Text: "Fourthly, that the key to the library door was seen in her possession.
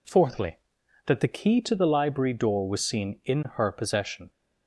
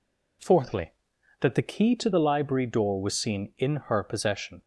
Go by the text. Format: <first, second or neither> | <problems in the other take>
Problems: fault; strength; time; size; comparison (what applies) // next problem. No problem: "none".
neither | none